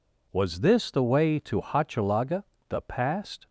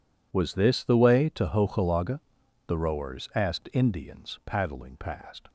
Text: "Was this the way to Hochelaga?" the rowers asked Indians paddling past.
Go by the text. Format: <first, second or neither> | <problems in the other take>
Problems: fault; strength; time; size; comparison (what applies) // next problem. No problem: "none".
second | skips "rowers asked Indians paddling"; at 2.8 s